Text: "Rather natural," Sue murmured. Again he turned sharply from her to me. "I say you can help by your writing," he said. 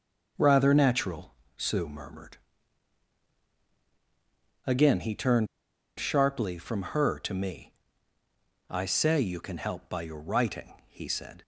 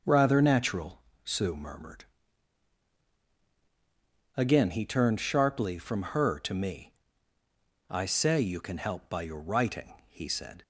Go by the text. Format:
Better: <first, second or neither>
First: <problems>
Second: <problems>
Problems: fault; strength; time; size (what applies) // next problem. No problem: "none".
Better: second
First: starts louder than the rest; until 1.6 s; 6.5 dB // pauses between "turned" and "sharply"; noticeable; at 5.4 s; 0.51 s long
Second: starts louder than the rest; until 1.2 s; 6.5 dB